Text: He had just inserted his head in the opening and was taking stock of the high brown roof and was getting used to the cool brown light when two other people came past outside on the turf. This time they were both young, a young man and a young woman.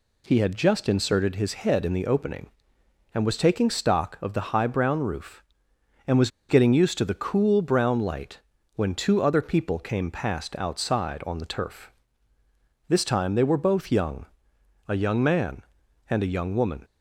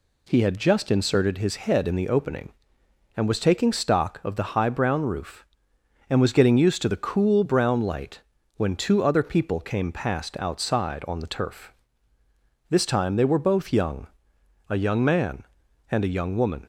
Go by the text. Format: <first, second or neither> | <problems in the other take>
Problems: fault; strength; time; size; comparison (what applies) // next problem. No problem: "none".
second | pauses between "was" and "getting"; slight; at 6.3 s; 0.19 s long // pauses between "light" and "when"; slight; at 8.3 s; 0.36 s long; slight in the second